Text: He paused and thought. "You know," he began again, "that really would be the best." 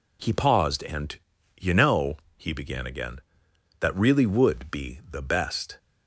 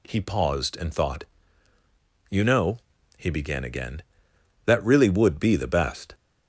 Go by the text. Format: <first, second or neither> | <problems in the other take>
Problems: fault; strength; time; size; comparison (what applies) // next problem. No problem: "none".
second | skips "thought"; at 1.3 s